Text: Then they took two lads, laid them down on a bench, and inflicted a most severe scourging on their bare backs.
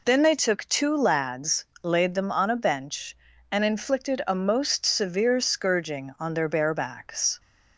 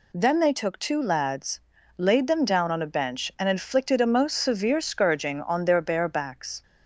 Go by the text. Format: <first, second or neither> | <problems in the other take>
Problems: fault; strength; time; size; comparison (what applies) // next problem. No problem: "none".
second | skips "down"; at 2.2 s